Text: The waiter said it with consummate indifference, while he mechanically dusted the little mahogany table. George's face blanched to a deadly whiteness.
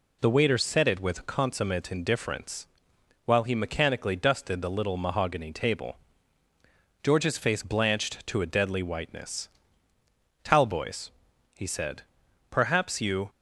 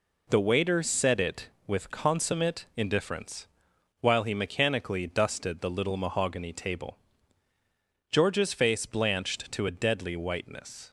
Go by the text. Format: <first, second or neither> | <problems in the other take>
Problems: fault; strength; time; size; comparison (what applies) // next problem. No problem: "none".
second | goes on to say "Talboys he said perhaps you"; strong; from 10.4 s on; 2.8 s long